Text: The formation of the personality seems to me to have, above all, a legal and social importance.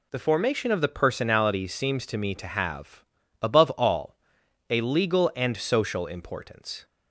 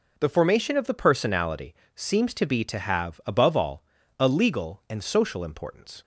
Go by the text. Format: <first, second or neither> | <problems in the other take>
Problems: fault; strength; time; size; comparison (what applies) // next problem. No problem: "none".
first | pauses between "personality" and "seems"; slight; at 1.7 s; 0.20 s long // says "be" for "me"; at 2.4 s